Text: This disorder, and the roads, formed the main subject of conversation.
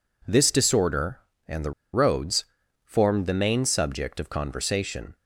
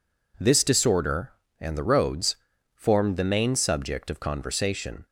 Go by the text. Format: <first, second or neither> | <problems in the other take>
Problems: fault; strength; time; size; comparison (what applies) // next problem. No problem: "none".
second | pauses between "the" and "roads"; slight; at 1.7 s; 0.22 s long